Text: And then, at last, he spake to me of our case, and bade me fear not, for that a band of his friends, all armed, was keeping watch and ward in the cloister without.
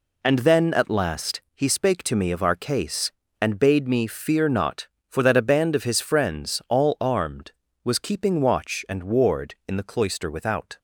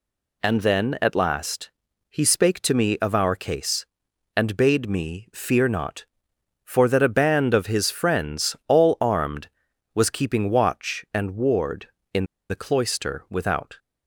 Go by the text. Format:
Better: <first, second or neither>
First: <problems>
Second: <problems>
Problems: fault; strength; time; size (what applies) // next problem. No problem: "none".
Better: first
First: none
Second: pauses between "in" and "the"; slight; at 12.2 s; 0.25 s long